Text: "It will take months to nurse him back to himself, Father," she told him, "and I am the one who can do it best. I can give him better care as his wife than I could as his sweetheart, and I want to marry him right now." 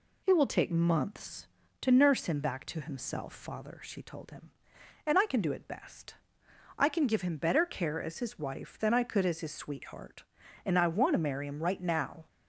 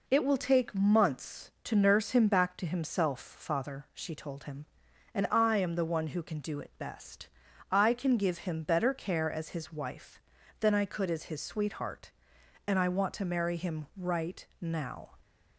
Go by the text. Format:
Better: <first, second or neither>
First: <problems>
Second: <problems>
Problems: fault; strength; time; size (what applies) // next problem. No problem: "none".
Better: second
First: skips "am the one who"; at 5.2 s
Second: none